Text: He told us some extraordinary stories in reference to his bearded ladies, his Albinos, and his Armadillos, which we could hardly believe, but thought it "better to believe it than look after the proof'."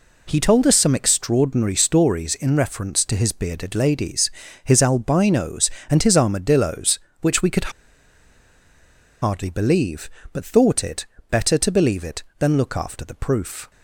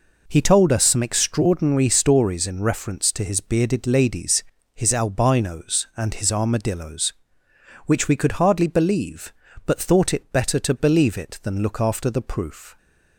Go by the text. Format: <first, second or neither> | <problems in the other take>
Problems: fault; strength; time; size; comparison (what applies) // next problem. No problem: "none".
second | pauses between "could" and "hardly"; strong; at 7.7 s; 1.5 s long // pauses between "it" and "better"; slight; at 11.0 s; 0.24 s long